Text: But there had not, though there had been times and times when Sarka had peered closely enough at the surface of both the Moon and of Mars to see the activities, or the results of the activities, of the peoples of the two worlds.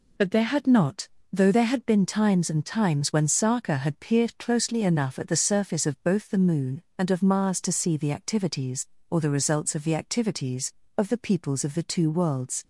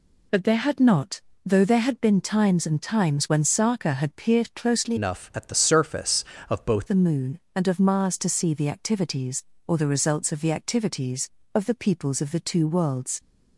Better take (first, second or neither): first